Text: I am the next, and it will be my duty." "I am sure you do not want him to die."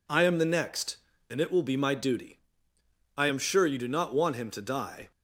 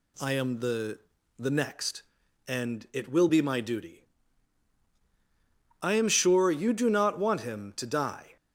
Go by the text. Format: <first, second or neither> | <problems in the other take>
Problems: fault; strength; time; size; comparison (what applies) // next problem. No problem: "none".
first | says "the" twice; at 1.3 s